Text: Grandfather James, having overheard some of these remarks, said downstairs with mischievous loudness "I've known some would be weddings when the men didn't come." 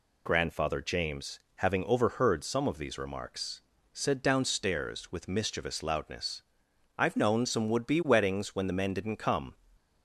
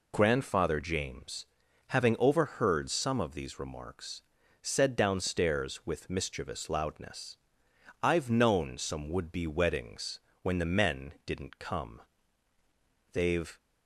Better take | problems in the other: first | pauses between "loudness" and "I've"; noticeable; at 7.3 s; 0.66 s long; noticeable in the first // pauses between "weddings" and "when"; slight; at 10.1 s; 0.24 s long // goes on to say "They've"; slight; from 13.1 s on; 0.44 s long

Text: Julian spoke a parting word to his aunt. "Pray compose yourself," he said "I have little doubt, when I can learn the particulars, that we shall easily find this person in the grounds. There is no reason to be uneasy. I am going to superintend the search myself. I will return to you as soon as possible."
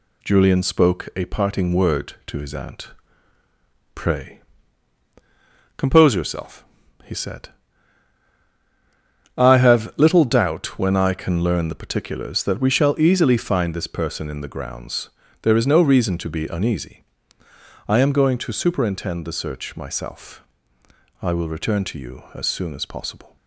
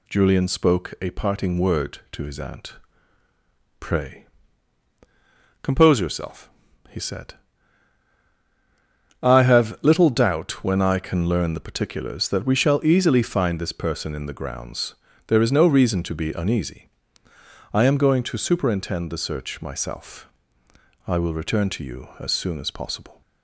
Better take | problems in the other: second | gets quieter; throughout; 3.5 dB // pauses between "Pray" and "compose"; strong; at 4.3 s; 1.3 s long; strong in the second // pauses between "said" and "I"; strong; at 7.4 s; 1.8 s long; strong in the second

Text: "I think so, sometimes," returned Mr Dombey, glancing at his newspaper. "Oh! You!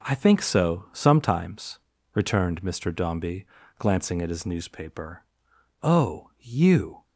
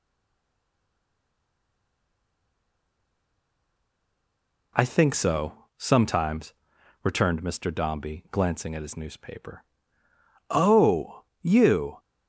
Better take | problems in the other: first | stays silent before the first word; strong; until 4.7 s; 4.7 s long

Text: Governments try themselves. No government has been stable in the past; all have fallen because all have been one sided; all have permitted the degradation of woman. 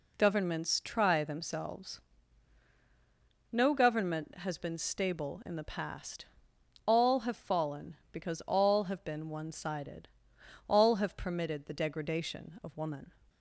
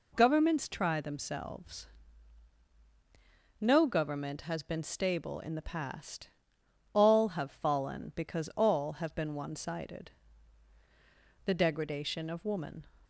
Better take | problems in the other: first | skips "all have permitted"; at 10.7 s

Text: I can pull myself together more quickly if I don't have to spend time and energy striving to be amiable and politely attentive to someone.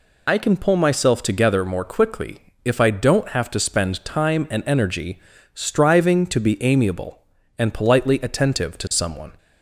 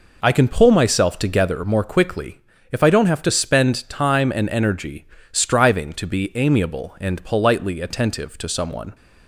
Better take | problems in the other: second | loses the start of "I"; at 0.2 s; 45 ms // pauses between "quickly" and "if"; slight; at 2.3 s; 0.26 s long; slight in the second // pauses between "energy" and "striving"; slight; at 5.2 s; 0.34 s long; slight in the second

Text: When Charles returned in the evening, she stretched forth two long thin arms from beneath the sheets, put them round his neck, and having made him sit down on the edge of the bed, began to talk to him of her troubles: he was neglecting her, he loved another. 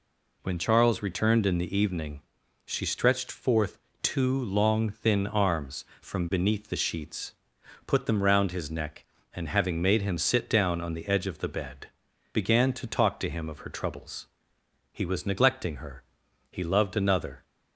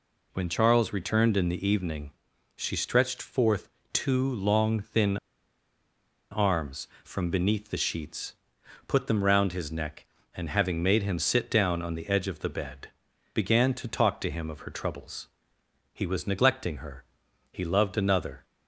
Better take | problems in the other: first | pauses between "forth" and "two"; slight; at 3.6 s; 0.24 s long; slight in the first // pauses between "thin" and "arms"; at 5.1 s; 1.1 s long

